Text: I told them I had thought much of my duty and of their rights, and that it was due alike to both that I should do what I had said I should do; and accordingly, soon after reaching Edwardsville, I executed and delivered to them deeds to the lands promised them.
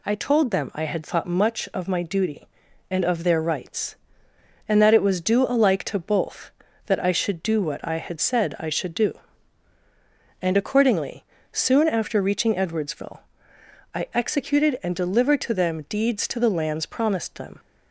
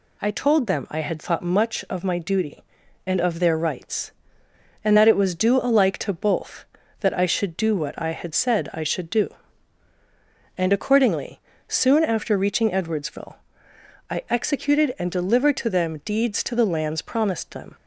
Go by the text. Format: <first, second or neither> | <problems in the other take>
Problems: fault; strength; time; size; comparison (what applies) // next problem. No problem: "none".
neither | none